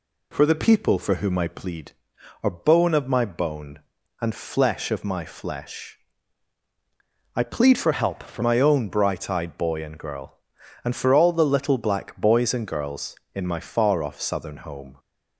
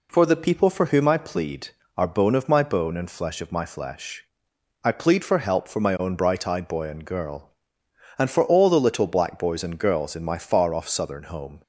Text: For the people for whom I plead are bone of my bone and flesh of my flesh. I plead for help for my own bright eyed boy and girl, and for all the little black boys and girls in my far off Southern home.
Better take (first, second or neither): second